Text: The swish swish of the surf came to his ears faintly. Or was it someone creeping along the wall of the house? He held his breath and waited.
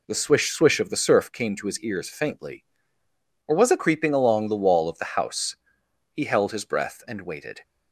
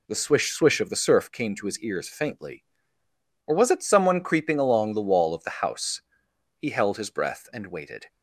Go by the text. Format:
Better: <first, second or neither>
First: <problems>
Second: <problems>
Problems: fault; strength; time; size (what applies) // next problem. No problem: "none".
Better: second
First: skips "someone"; at 3.7 s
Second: none